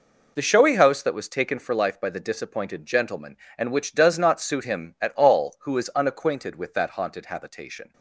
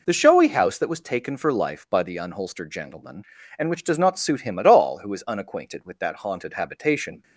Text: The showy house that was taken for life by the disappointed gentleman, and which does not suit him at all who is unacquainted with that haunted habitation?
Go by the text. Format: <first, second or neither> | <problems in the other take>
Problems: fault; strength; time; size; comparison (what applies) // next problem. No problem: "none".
first | says "unholstered" for "disappointed"; at 2.1 s